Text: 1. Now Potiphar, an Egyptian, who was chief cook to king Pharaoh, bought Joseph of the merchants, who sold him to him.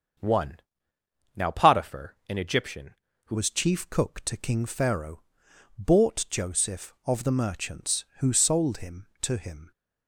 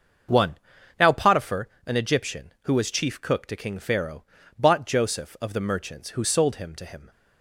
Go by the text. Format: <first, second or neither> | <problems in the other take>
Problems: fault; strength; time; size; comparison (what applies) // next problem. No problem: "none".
second | starts louder than the rest; until 1.9 s; 6.5 dB; also in the second // changes voice at "was"; from 3.3 s on; 6.4 s long